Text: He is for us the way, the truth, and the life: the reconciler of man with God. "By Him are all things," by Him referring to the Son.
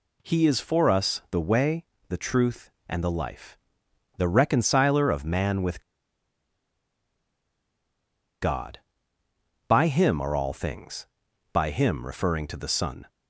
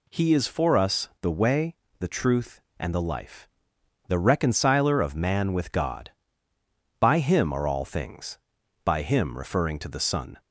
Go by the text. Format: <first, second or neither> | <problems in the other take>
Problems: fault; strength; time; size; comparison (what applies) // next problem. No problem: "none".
second | pauses between "with" and "God"; strong; at 5.7 s; 2.6 s long